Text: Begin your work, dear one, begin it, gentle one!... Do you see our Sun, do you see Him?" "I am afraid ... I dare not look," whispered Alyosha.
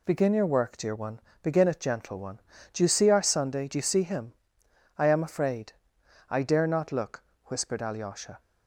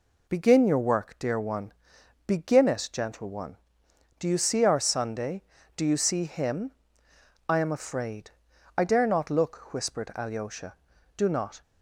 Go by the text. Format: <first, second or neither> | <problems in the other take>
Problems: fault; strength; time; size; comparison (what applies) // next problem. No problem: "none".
first | goes on to say "Do not"; slight; from 11.1 s on; 0.46 s long